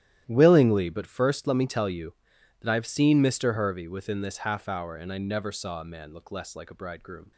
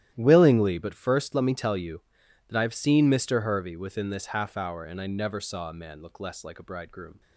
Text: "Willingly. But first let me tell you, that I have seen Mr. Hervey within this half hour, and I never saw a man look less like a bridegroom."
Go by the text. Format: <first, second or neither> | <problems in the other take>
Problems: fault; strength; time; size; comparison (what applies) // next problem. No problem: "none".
neither | starts louder than the rest; strong; the same in both